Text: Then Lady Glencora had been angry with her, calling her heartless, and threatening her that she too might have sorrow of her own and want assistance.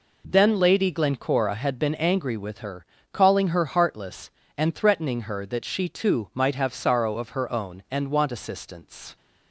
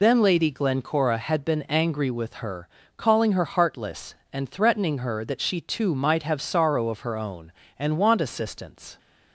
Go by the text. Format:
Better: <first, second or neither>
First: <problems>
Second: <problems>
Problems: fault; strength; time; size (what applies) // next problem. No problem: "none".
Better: first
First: none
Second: loses the start of "Then"; at 0.0 s; 55 ms